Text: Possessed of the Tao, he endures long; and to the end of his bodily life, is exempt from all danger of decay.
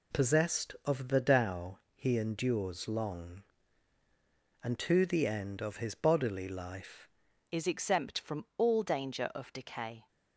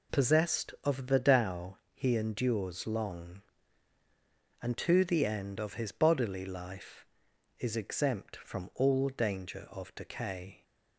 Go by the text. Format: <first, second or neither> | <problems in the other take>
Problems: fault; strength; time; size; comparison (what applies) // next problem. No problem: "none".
second | changes voice at "is"; from 7.5 s on; 2.5 s long